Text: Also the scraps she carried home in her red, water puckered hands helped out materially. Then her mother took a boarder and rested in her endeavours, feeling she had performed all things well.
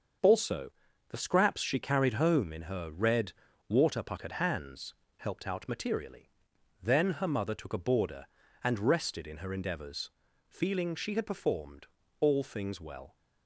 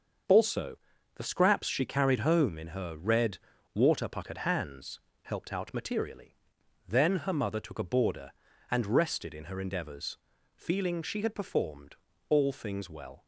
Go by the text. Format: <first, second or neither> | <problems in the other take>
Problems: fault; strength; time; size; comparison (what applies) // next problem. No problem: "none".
neither | starts louder than the rest; the same in both // pauses between "Also" and "the"; the same in both // pauses between "hands" and "helped"; slight; the same in both // pauses between "performed" and "all"; slight; the same in both